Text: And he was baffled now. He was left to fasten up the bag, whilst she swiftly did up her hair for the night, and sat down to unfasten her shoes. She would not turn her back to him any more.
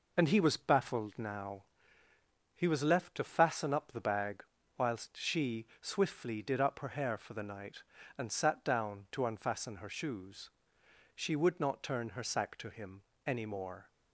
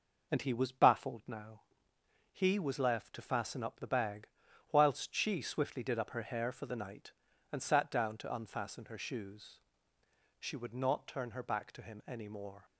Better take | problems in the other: second | says "sack" for "back"; at 12.2 s // pauses between "him" and "any"; slight; at 13.0 s; 0.24 s long

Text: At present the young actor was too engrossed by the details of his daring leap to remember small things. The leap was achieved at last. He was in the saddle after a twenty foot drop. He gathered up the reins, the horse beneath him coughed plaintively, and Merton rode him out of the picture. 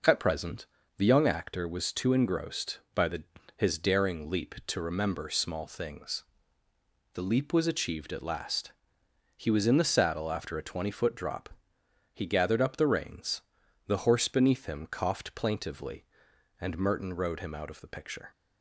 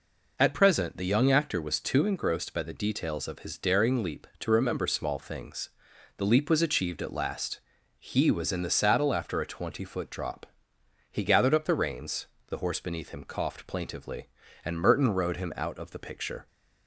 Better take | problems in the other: second | pauses between "present" and "the"; slight; at 0.6 s; 0.32 s long // skips "details of"; at 3.3 s

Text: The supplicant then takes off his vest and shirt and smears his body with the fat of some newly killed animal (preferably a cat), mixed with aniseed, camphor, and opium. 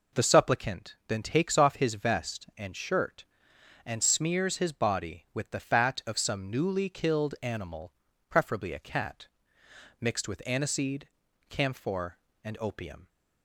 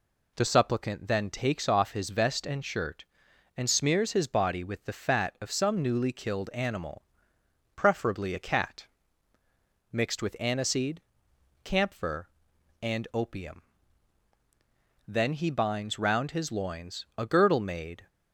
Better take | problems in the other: first | goes on to say "Then he binds round his loins a girdle made"; strong; from 15.0 s on; 3.0 s long

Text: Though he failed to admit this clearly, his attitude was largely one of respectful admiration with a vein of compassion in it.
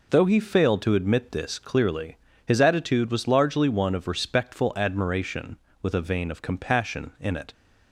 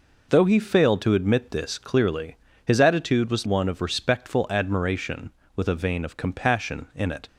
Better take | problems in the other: first | skips "largely"; at 3.4 s

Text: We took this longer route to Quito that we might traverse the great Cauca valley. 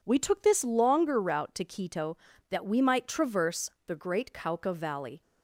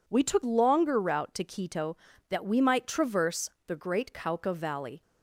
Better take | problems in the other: first | skips "this"; at 0.4 s // pauses between "traverse" and "the"; slight; at 3.4 s; 0.18 s long; slight in the first

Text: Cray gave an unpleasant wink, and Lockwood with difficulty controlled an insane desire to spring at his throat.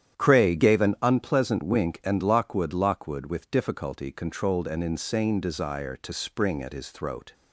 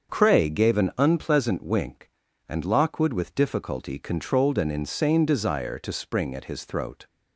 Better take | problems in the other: second | starts louder than the rest; strong; until 1.2 s; 10 dB; also in the second // says "Lockwood" twice; at 2.7 s

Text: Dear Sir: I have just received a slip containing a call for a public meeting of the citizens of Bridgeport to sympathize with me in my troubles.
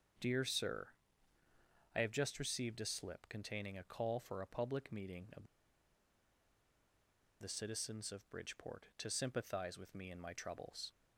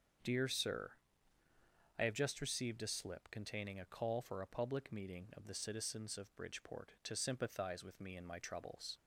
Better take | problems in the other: second | starts louder than the rest; until 2.2 s; 6.5 dB; also in the second // pauses between "of" and "the"; strong; at 5.4 s; 1.9 s long

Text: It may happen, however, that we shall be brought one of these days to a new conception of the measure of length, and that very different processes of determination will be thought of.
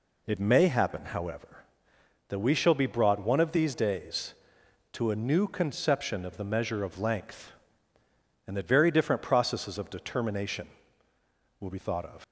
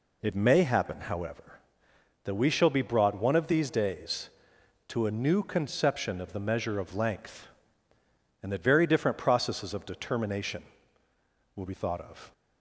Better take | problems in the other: second | leaves "of" unfinished; at 12.2 s; 125 ms

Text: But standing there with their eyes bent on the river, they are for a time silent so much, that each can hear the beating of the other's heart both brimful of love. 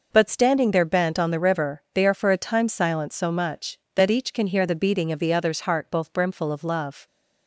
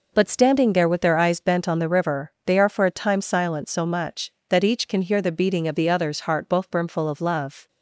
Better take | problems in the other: second | skips "with their eyes"; at 0.8 s

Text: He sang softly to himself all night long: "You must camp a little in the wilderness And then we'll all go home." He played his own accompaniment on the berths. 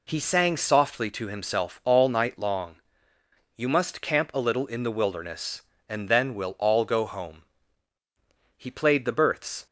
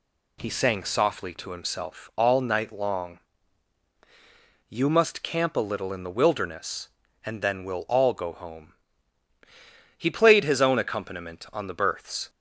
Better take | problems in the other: second | skips "his own accompaniment on"; at 9.0 s

